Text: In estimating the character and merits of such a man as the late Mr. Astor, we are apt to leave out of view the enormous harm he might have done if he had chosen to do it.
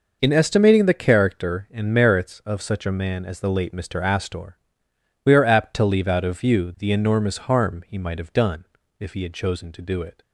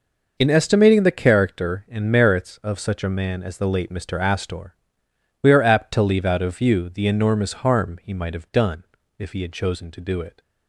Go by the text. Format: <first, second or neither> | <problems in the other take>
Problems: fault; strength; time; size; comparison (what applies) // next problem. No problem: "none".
neither | pauses between "done" and "if"; slight; the same in both